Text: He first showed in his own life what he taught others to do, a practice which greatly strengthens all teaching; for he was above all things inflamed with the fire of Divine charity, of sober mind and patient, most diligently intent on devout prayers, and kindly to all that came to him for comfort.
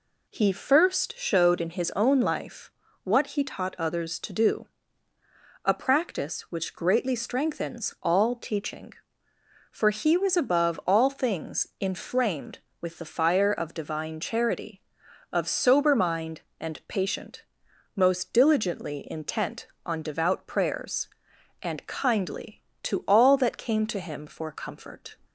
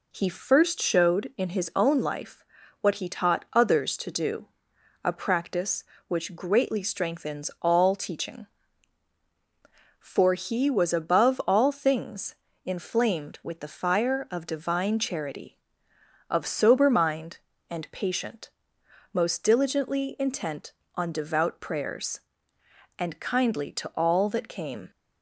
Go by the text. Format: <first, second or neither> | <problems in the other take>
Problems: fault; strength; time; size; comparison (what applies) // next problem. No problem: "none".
first | pauses between "life" and "what"; at 2.4 s; 0.38 s long; slight in the first // pauses between "things" and "inflamed"; slight; at 12.3 s; 0.32 s long // stops before "to him for comfort"; at 24.9 s